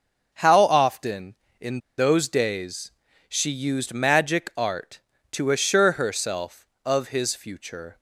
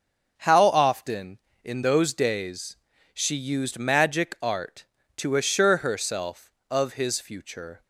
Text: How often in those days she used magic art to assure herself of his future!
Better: second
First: starts louder than the rest; until 1.3 s; 6 dB // pauses between "in" and "those"; slight; at 1.7 s; 0.19 s long // pauses between "days" and "she"; slight; at 2.9 s; 0.36 s long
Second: starts louder than the rest; until 1.3 s; 6.5 dB // pauses between "days" and "she"; slight; at 2.7 s; 0.36 s long

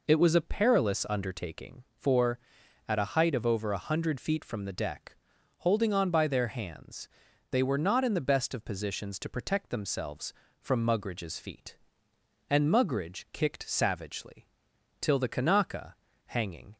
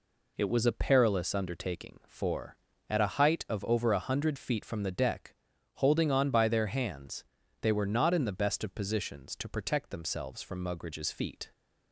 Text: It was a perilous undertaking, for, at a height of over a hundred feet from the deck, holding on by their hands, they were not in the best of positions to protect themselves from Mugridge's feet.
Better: second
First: goes on to say "And Mugridge kicked savagely till the Kanaka hanging"; strong; from 12.4 s on; 4.2 s long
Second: none

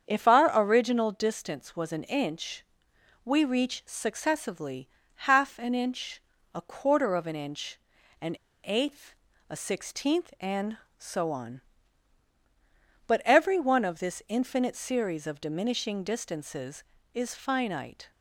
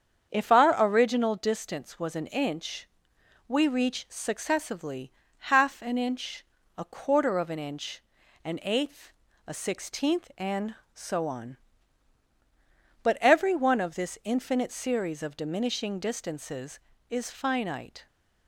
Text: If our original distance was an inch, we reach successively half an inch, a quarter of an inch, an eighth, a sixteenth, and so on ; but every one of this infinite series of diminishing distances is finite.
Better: second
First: starts louder than the rest; strong; until 1.1 s; 7 dB // pauses between "successively" and "half"; slight; at 4.8 s; 0.28 s long // pauses between "an" and "eighth"; slight; at 8.3 s; 0.27 s long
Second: starts louder than the rest; strong; until 1.4 s; 7 dB // pauses between "successively" and "half"; slight; at 5.1 s; 0.28 s long

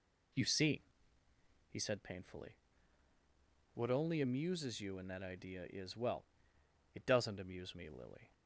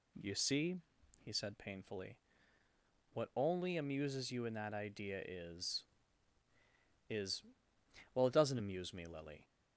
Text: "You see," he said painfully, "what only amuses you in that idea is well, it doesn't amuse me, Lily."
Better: first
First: none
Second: says "is" twice; at 7.0 s

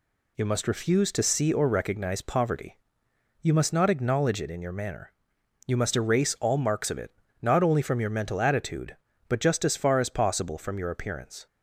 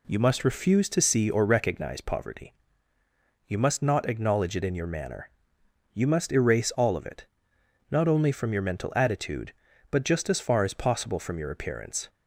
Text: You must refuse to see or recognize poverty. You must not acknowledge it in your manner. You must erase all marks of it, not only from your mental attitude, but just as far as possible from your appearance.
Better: first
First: none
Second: skips "marks"; at 6.9 s

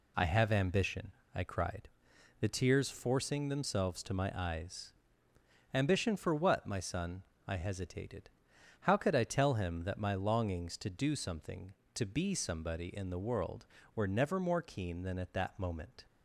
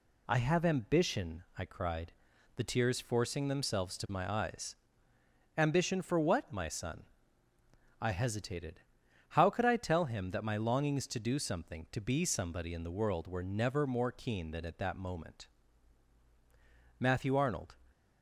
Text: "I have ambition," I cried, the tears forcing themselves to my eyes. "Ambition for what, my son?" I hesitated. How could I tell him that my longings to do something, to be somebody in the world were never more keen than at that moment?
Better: first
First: none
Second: goes on to say "Matthew Arnold"; noticeable; from 17.0 s on; 0.76 s long

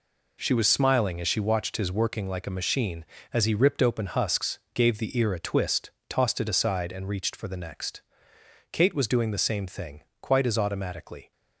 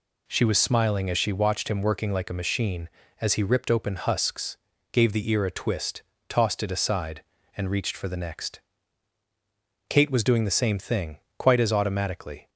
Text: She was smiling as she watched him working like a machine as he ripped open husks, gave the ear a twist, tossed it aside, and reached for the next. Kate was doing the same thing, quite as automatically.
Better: second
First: says "his" for "him"; at 1.7 s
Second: none

